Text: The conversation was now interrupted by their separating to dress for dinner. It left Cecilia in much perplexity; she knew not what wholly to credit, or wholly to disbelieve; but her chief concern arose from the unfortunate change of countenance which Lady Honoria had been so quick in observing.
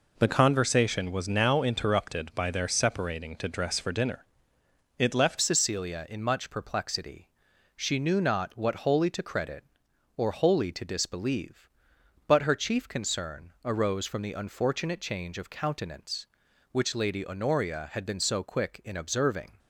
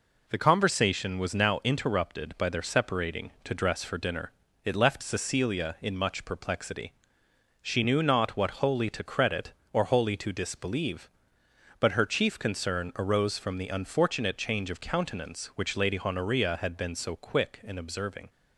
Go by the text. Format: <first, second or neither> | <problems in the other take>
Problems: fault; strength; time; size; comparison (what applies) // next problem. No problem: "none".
second | changes voice at "Cecilia"; from 5.4 s on; 14.1 s long